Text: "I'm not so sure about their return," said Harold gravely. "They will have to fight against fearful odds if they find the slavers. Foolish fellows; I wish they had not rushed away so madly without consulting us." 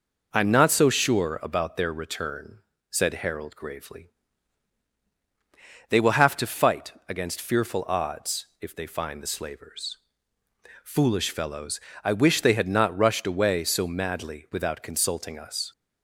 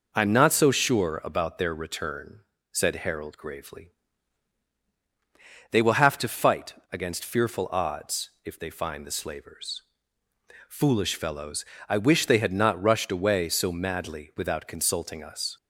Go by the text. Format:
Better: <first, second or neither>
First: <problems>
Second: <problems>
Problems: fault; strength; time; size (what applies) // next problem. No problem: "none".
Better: neither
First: pauses between "fight" and "against"; slight; at 6.9 s; 0.16 s long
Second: pauses between "fight" and "against"; slight; at 6.7 s; 0.18 s long